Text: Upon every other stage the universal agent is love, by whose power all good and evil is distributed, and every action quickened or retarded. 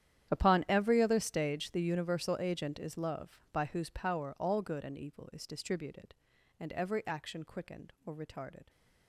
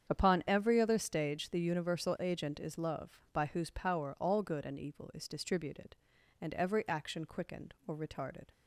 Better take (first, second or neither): second